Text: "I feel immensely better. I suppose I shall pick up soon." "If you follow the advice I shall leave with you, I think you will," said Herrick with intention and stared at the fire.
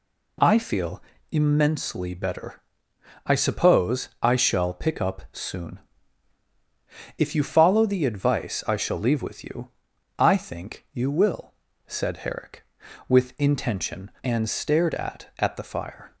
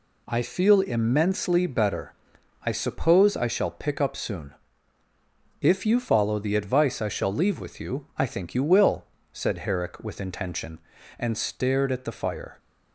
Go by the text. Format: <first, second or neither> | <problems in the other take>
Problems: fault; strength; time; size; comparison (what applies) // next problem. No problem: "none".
second | pauses between "feel" and "immensely"; slight; at 1.0 s; 0.30 s long // says "at" twice; at 15.3 s